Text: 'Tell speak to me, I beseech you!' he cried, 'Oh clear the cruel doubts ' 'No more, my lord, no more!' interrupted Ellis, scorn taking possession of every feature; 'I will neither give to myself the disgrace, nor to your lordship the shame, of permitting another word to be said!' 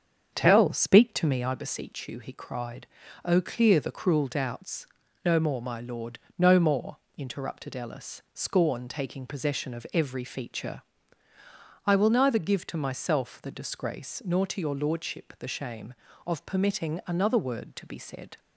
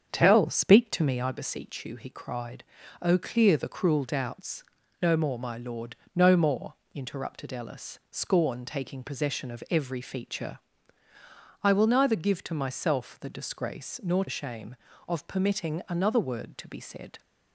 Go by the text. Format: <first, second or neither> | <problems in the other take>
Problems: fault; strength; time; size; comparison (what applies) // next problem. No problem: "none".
first | starts louder than the rest; strong; until 1.1 s; 7.5 dB; strong in the first // skips "to your lordship the"; at 14.2 s